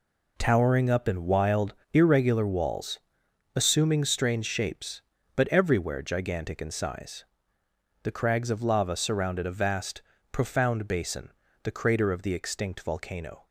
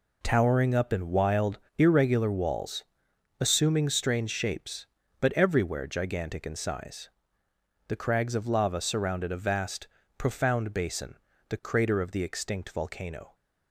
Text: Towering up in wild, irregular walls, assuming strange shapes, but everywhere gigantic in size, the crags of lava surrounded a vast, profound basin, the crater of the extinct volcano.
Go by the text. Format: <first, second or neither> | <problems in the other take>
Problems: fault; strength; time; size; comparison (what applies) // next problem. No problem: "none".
neither | none